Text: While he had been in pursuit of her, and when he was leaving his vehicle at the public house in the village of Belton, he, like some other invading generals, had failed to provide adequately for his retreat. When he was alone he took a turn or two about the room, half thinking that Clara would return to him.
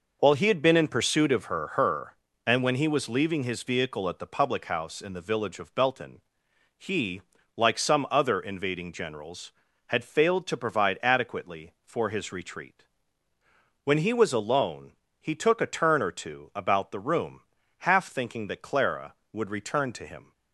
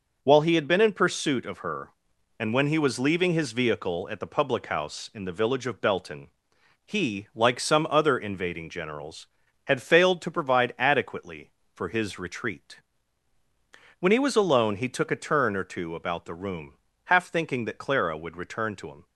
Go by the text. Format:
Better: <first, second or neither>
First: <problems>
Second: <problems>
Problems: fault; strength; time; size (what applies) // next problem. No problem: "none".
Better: second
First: says "her" twice; at 1.6 s // pauses between "alone" and "he"; slight; at 14.9 s; 0.30 s long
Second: none